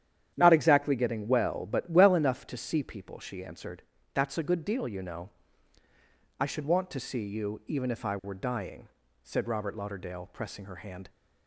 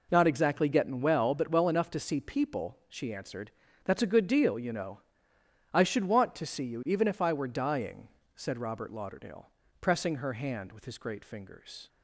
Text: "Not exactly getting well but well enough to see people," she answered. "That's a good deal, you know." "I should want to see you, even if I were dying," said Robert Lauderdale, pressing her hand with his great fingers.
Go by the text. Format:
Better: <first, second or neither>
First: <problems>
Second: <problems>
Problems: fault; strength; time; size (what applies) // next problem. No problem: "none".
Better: second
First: starts louder than the rest; strong; until 1.3 s; 10 dB // stops before "with his great fingers"; at 11.0 s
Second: none